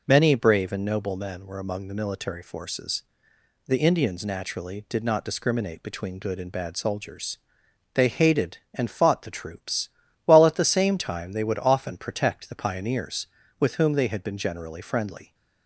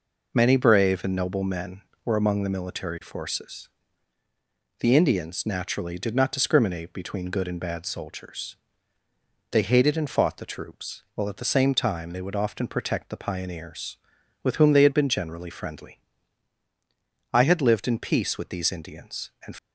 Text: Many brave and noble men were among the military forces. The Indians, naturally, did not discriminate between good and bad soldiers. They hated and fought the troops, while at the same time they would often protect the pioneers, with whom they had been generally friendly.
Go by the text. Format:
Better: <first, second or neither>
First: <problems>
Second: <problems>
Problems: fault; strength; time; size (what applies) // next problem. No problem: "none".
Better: first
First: none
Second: goes on to say "I had lived in peace with these Indians and"; strong; from 17.3 s on; 2.2 s long